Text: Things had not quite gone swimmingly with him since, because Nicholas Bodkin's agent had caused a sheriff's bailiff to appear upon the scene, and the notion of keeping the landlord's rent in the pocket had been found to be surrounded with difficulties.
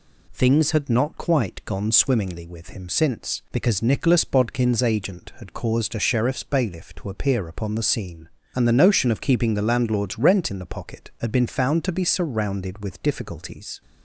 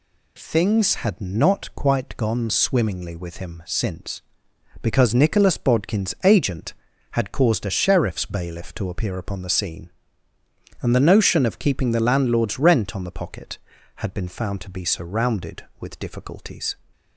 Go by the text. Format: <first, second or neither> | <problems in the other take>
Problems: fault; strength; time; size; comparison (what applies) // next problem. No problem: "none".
first | says "on" for "in"; at 12.9 s